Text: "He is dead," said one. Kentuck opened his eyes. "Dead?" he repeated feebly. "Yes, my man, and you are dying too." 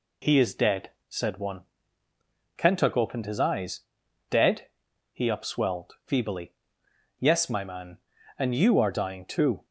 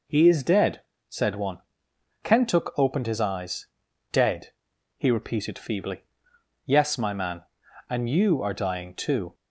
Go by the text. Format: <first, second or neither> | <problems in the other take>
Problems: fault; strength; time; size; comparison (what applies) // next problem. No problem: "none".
second | says "upswelled" for "repeated"; at 5.2 s